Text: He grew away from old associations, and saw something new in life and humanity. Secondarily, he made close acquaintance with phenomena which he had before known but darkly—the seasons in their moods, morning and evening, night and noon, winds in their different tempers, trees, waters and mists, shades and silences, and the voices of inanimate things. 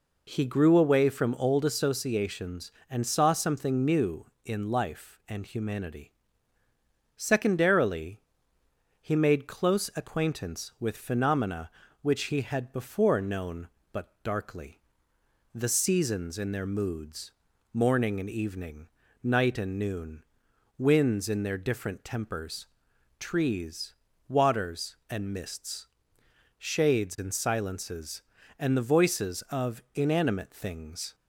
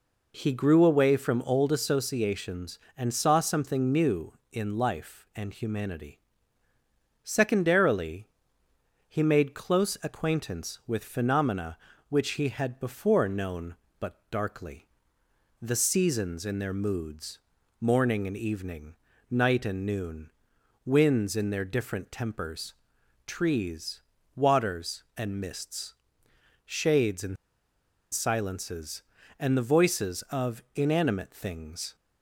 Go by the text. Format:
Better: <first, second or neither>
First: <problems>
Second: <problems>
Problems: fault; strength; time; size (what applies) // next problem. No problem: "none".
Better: first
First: none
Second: pauses between "and" and "silences"; noticeable; at 27.3 s; 0.76 s long